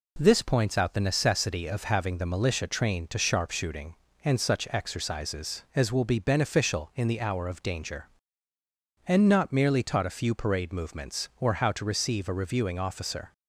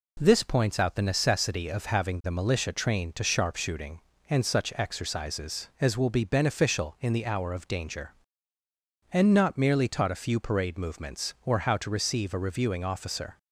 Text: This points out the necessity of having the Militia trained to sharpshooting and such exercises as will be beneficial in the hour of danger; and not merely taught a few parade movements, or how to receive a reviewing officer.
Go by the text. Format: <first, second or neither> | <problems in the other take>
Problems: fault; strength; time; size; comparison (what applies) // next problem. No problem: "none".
neither | none